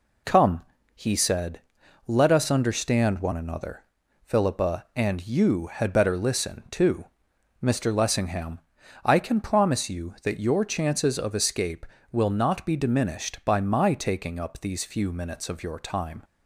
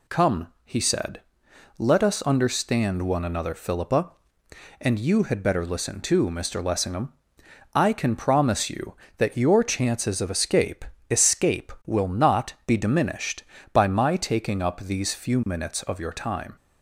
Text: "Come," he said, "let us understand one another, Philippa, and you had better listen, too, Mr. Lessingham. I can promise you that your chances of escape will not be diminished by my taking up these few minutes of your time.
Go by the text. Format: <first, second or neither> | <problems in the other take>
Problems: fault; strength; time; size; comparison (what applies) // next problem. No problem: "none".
first | says "escape" twice; at 11.0 s